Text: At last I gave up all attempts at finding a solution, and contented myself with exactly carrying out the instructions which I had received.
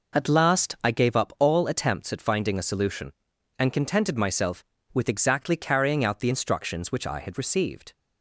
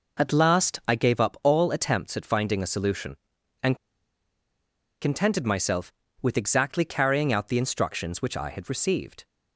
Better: first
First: none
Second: pauses between "and" and "contented"; strong; at 3.7 s; 1.2 s long

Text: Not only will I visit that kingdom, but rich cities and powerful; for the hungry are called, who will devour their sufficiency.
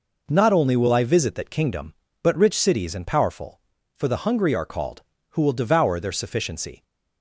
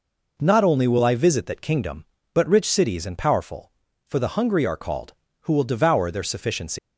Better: first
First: none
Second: leaves "sufficiency" unfinished; at 6.7 s; 155 ms

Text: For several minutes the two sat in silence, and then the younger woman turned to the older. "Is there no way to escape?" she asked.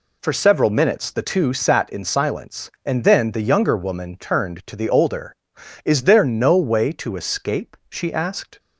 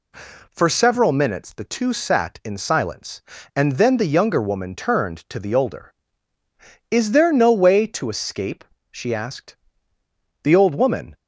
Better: first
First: none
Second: goes on to say "The old woman"; noticeable; from 10.4 s on; 0.74 s long

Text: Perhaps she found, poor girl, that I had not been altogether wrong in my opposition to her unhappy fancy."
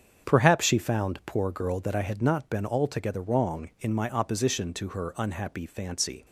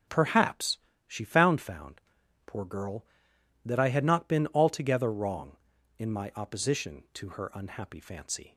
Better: first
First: starts louder than the rest; strong; until 1.3 s; 7.5 dB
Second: starts louder than the rest; noticeable; until 1.3 s; 6 dB // pauses between "Perhaps" and "she"; slight; at 0.7 s; 0.28 s long // says "found" twice; at 1.6 s

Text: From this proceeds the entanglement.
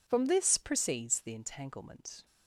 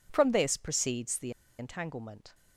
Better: first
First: none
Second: pauses between "the" and "entanglement"; slight; at 1.3 s; 0.28 s long

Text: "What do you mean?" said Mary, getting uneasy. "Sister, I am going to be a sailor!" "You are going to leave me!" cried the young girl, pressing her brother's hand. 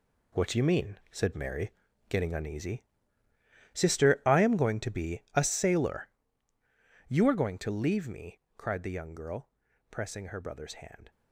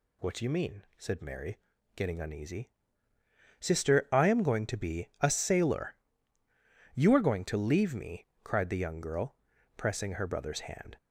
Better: second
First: gets quieter; strong; throughout; 10 dB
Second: none

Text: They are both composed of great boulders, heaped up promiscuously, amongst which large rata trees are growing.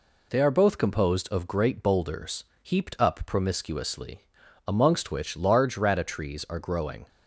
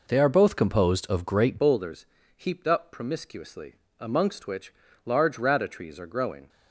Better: first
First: none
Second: changes voice at "boulders"; from 1.5 s on; 4.9 s long // pauses between "which" and "large"; slight; at 4.7 s; 0.32 s long

